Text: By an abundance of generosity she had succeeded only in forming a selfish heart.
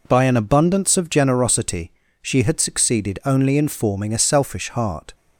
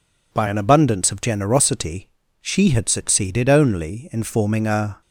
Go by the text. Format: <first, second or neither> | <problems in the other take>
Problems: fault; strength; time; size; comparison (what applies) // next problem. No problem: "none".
first | pauses between "generosity" and "she"; slight; at 2.0 s; 0.34 s long; slight in the first // stops before "selfish heart"; at 5.0 s